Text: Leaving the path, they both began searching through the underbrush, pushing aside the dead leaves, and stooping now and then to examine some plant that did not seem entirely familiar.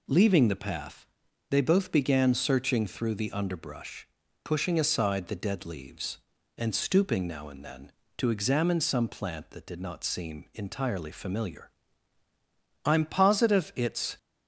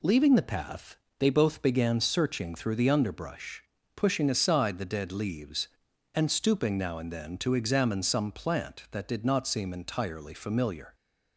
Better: second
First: goes on to say "I'm positive it's"; from 12.8 s on; 1.3 s long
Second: none

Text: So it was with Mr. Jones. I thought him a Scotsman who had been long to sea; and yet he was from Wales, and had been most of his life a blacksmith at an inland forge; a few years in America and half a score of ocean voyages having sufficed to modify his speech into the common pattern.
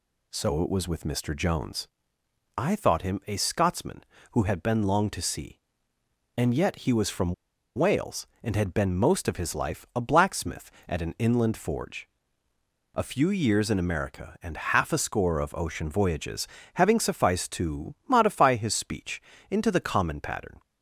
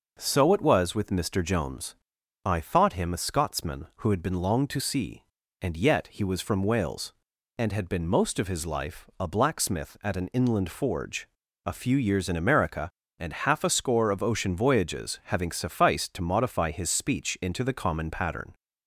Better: second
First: pauses between "from" and "Wales"; at 7.3 s; 0.42 s long // pauses between "voyages" and "having"; slight; at 16.4 s; 0.28 s long // pauses between "speech" and "into"; slight; at 19.2 s; 0.28 s long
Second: none

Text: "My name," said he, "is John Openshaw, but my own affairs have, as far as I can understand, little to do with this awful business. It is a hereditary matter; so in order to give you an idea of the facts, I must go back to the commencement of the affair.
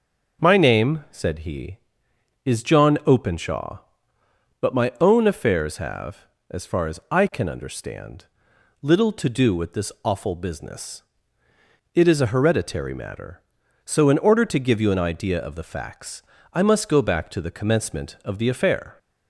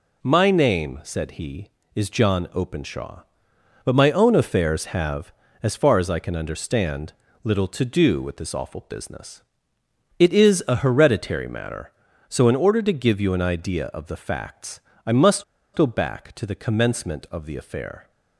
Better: first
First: none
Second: pauses between "must" and "go"; slight; at 15.4 s; 0.32 s long

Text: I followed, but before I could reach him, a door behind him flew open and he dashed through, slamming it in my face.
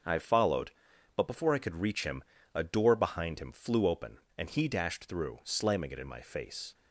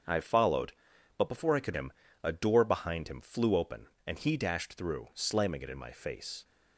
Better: first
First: starts louder than the rest; until 1.5 s; 6.5 dB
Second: starts louder than the rest; until 1.5 s; 7 dB // skips "reach"; at 1.7 s

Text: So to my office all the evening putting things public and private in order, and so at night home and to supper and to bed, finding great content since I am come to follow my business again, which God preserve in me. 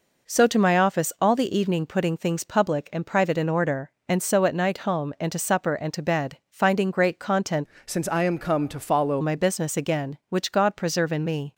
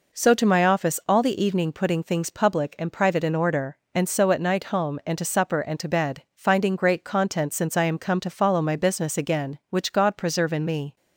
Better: second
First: changes voice from "since" to "follow"; from 7.8 to 9.2 s; 1.4 s long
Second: none

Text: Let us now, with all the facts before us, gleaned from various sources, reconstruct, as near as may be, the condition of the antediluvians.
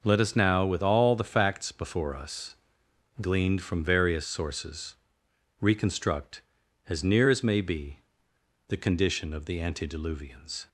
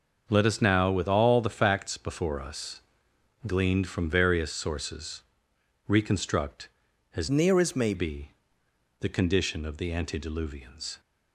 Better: first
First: none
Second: starts louder than the rest; noticeable; until 1.2 s; 6 dB // changes voice from "near" to "may"; from 7.3 to 7.9 s; 0.6 s long

